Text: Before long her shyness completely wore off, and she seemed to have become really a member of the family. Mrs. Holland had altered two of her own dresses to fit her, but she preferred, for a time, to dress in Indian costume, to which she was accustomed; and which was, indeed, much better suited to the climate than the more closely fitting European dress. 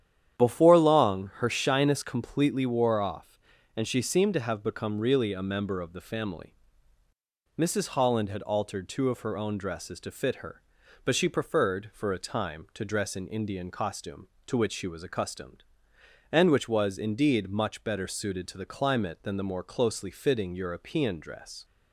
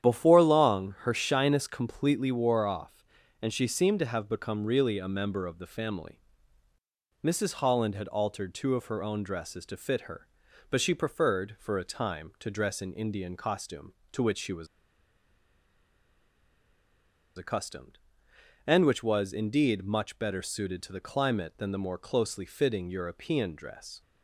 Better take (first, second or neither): first